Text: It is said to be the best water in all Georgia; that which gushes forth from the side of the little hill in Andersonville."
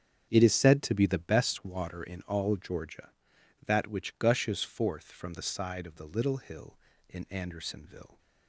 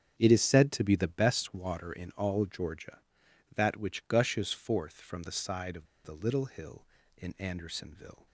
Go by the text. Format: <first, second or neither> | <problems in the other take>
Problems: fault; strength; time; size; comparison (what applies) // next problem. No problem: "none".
first | starts louder than the rest; strong; until 1.1 s; 8 dB; strong in the first // pauses between "of" and "the"; slight; at 5.8 s; 0.18 s long